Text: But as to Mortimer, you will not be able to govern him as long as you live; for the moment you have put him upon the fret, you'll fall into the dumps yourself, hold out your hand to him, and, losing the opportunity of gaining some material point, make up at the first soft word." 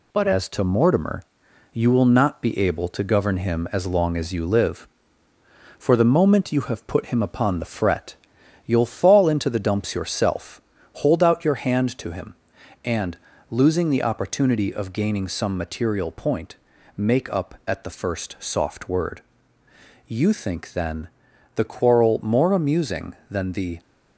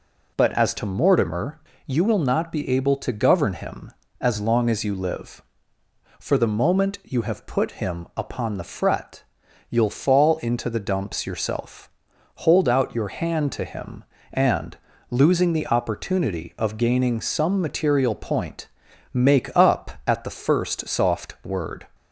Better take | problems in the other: second | goes on to say "You think then the quarrel more amusing than the"; strong; from 20.0 s on; 3.7 s long

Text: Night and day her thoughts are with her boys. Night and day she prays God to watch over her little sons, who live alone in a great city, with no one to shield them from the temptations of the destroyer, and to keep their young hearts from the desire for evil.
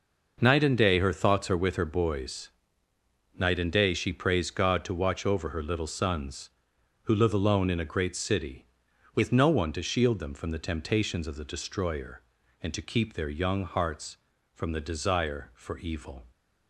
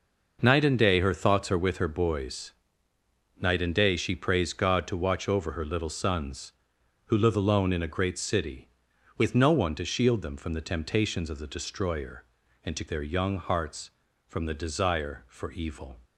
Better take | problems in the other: first | skips "keep"; at 12.8 s

